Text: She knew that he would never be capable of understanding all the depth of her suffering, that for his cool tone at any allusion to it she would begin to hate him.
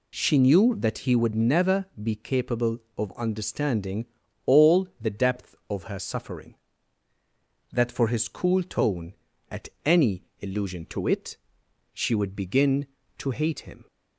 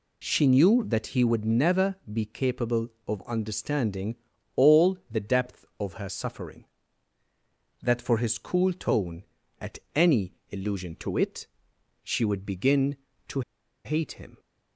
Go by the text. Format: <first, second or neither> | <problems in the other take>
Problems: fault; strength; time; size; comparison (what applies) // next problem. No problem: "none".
first | pauses between "understanding" and "all"; at 4.1 s; 0.40 s long; also in the first // pauses between "at" and "any"; slight; at 9.7 s; 0.18 s long; slight in the first // pauses between "any" and "allusion"; slight; at 10.3 s; 0.22 s long; slight in the first // pauses between "it" and "she"; noticeable; at 11.4 s; 0.58 s long; noticeable in the first // pauses between "to" and "hate"; at 13.4 s; 0.44 s long